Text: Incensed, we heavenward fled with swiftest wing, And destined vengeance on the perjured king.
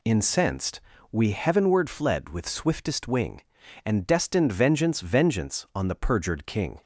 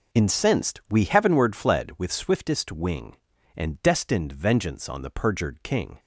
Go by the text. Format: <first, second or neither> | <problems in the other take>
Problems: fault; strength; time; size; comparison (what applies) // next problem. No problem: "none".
second | says "vengeance" twice; at 5.0 s